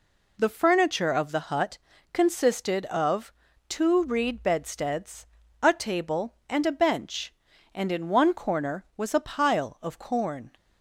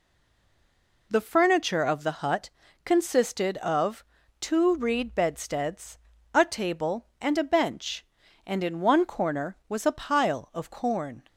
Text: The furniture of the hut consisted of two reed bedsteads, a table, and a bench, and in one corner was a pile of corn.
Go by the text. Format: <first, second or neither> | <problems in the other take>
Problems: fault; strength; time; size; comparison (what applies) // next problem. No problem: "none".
first | stays silent before the first word; until 1.1 s; 1.1 s long // pauses between "hut" and "consisted"; slight; at 2.4 s; 0.34 s long; slight in the first // pauses between "of" and "two"; at 4.0 s; 0.38 s long; also in the first